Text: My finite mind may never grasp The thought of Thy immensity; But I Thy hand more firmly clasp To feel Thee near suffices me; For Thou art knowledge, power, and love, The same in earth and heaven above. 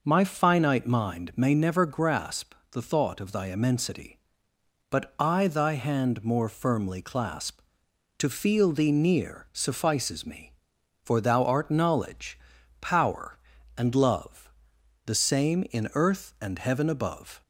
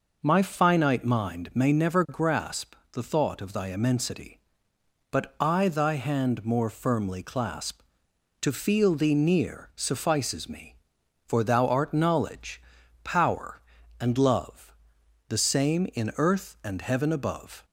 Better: neither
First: pauses between "grasp" and "The"; slight; at 2.5 s; 0.18 s long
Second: pauses between "grasp" and "The"; slight; at 2.7 s; 0.18 s long

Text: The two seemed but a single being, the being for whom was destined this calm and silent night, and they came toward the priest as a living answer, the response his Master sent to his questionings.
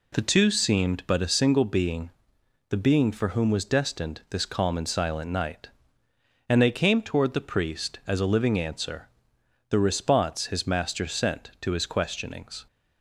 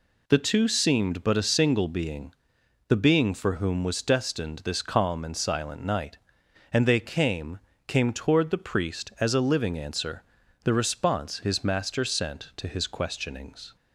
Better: first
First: none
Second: says "came" twice; at 7.8 s

